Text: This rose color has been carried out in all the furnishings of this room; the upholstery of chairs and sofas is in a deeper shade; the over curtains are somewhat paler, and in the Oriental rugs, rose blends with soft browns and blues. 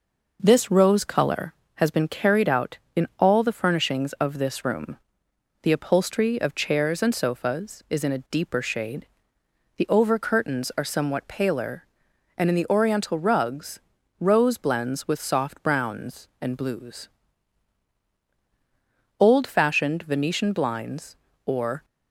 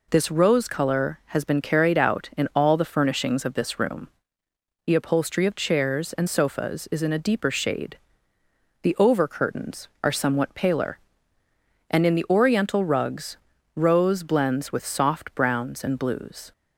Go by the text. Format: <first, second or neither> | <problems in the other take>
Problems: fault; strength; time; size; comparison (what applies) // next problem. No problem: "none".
second | goes on to say "Old fashioned Venetian blinds or"; strong; from 19.1 s on; 2.6 s long